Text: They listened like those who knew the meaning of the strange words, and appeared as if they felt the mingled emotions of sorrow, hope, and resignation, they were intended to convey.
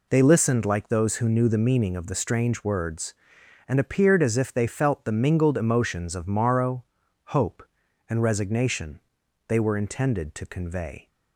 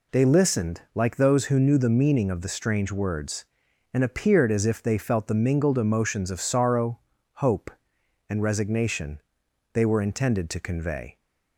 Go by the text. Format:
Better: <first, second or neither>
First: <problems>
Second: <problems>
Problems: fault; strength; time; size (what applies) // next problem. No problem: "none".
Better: second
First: says "morrow" for "sorrow"; at 6.2 s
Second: none